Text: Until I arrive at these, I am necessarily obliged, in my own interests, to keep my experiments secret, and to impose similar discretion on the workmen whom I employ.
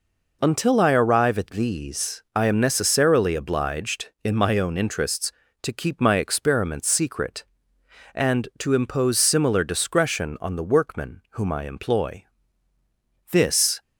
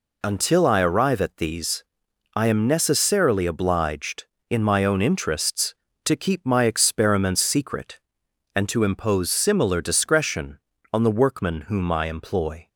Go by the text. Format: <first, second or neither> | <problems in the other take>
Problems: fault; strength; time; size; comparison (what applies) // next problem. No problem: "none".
second | goes on to say "This"; from 13.3 s on; 0.50 s long